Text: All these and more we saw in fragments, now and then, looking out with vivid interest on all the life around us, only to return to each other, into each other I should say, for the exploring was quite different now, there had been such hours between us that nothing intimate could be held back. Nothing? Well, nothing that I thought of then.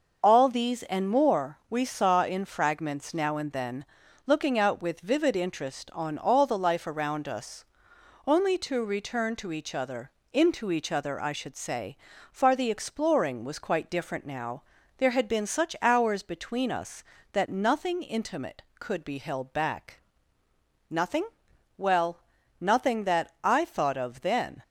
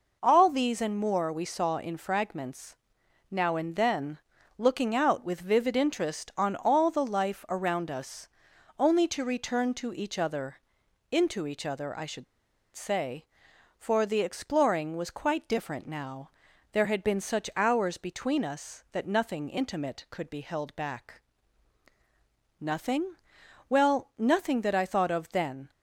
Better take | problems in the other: first | pauses between "should" and "say"; noticeable; at 12.2 s; 0.50 s long

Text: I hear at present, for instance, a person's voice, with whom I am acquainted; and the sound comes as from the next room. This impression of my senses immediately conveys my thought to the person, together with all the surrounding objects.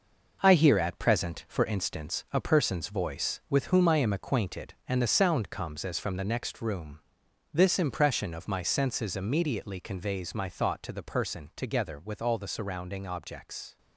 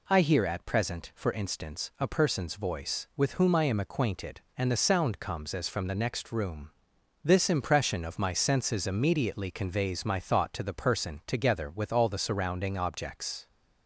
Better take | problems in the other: second | gets quieter; strong; throughout; 7.5 dB

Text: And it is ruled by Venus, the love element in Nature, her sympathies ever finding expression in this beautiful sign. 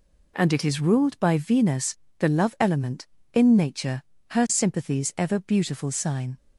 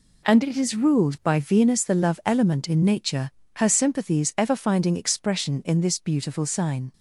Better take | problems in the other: second | skips "finding expression in this"; at 5.3 s

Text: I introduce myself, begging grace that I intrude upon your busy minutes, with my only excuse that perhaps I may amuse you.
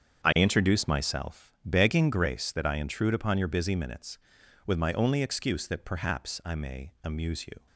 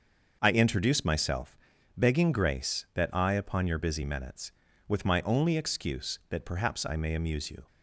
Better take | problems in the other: first | starts louder than the rest; until 1.4 s; 6.5 dB; strong in the first // skips "intrude"; at 3.3 s

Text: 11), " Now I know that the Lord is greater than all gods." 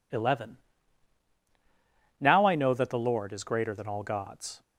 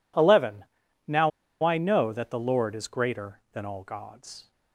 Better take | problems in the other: first | pauses between "Now" and "I"; slight; at 1.3 s; 0.33 s long

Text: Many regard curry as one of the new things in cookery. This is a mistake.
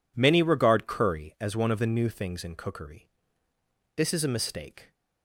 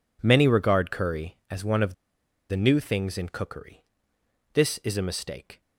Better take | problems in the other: first | pauses between "of" and "the"; noticeable; at 1.9 s; 0.55 s long

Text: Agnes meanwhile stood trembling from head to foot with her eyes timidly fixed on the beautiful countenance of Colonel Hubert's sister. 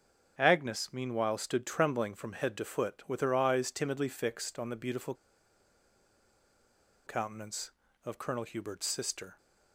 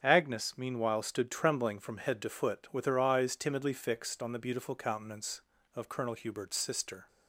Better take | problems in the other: second | starts louder than the rest; strong; until 1.3 s; 7 dB; also in the second // pauses between "beautiful" and "countenance"; strong; at 5.1 s; 1.9 s long

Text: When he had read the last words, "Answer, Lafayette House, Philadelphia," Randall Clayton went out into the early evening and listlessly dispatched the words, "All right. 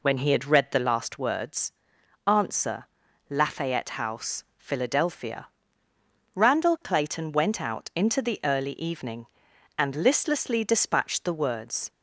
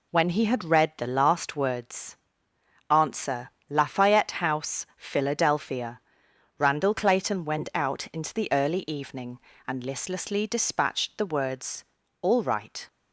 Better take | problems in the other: second | stops before "All right"; at 11.8 s

